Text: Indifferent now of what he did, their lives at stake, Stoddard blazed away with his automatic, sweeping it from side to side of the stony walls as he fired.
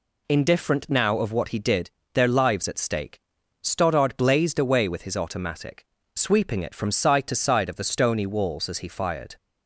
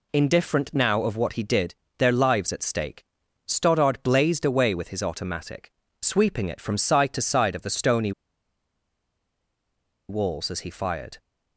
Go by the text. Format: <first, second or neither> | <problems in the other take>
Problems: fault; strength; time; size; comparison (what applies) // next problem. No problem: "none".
first | pauses between "stony" and "walls"; strong; at 8.1 s; 1.9 s long